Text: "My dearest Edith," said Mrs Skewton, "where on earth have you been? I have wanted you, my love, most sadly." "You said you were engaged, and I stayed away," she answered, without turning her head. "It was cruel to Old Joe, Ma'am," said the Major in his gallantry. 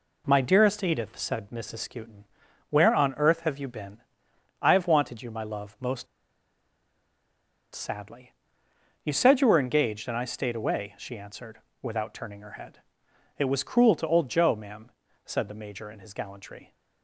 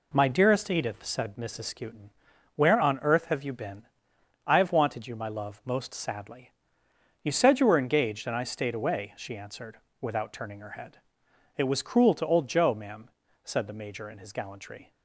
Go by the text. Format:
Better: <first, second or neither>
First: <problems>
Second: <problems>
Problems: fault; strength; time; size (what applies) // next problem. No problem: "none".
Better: second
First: pauses between "most" and "sadly"; strong; at 6.0 s; 1.6 s long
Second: none